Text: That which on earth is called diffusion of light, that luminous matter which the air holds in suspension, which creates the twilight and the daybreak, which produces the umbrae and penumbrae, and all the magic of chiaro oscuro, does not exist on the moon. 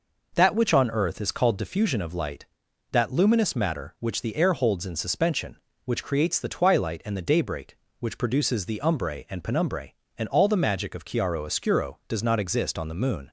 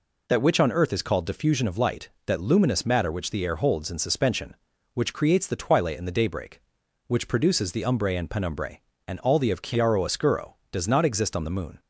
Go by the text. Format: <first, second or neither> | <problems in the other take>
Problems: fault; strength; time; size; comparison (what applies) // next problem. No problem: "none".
first | skips "magic"; at 9.5 s